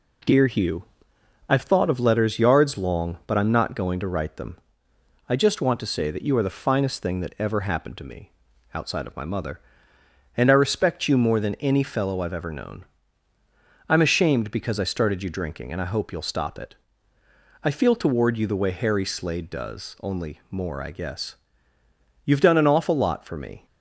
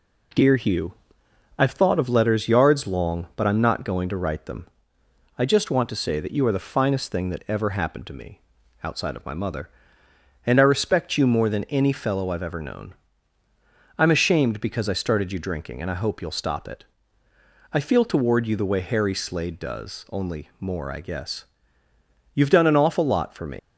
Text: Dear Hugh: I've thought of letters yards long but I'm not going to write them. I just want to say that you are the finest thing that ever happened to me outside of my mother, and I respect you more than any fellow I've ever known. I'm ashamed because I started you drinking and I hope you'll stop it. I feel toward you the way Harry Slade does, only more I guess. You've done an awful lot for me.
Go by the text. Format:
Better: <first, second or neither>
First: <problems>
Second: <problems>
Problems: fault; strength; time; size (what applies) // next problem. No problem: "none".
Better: first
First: pauses between "me" and "outside"; at 8.3 s; 0.42 s long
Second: pauses between "me" and "outside"; at 8.4 s; 0.42 s long // leaves "me" unfinished; at 23.5 s; 150 ms